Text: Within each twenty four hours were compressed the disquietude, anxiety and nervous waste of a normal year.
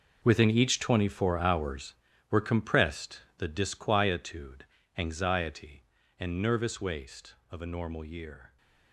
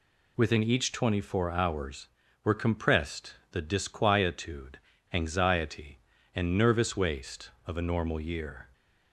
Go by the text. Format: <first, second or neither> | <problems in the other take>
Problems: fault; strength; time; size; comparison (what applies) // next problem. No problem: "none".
second | gets quieter; strong; throughout; 14.5 dB // pauses between "compressed" and "the"; slight; at 3.2 s; 0.16 s long; slight in the second